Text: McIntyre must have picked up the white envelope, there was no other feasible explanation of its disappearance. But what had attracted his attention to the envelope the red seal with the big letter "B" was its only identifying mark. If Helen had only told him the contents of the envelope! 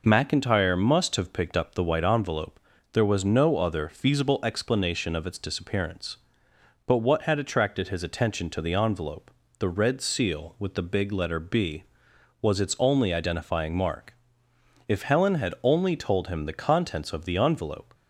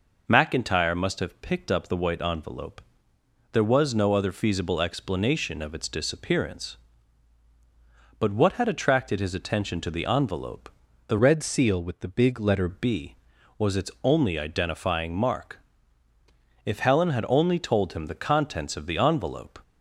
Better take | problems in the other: first | pauses between "envelope" and "the"; at 10.6 s; 0.38 s long; slight in the first // changes voice from "red" to "letter"; from 11.1 to 12.6 s; 1.5 s long

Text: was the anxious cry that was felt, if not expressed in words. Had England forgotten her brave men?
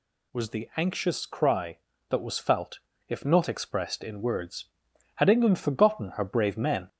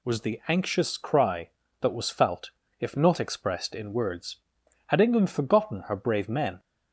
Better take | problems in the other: second | gets louder; slight; throughout; 2 dB

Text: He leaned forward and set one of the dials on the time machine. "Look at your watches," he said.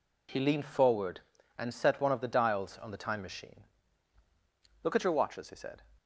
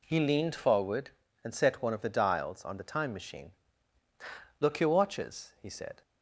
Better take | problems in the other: first | skips "at"; at 4.8 s

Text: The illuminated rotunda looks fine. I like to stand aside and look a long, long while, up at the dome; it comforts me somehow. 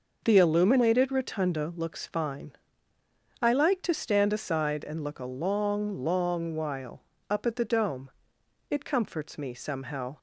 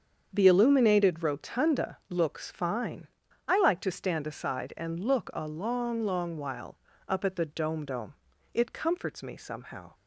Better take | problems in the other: first | starts louder than the rest; strong; until 1.3 s; 7.5 dB // says "dome" twice; at 7.8 s

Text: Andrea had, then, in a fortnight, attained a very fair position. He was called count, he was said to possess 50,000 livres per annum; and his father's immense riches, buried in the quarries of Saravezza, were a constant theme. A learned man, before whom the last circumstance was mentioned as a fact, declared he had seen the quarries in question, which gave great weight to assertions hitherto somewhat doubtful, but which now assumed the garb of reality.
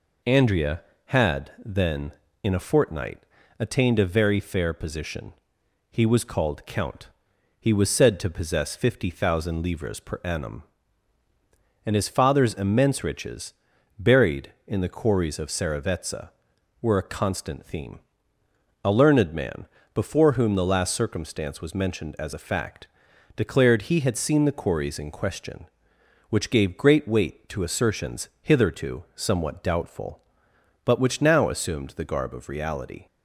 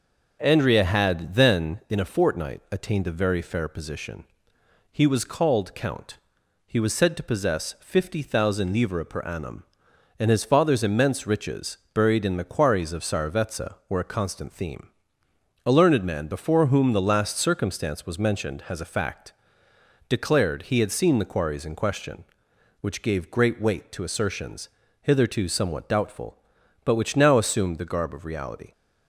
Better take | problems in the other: first | says "has" for "as"; at 18.6 s // pauses between "assertions" and "hitherto"; slight; at 24.6 s; 0.32 s long

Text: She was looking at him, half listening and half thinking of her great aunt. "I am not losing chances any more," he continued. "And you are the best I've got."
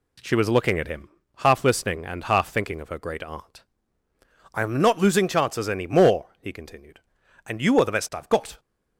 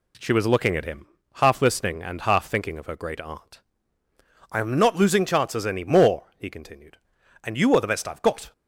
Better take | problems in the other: neither | none

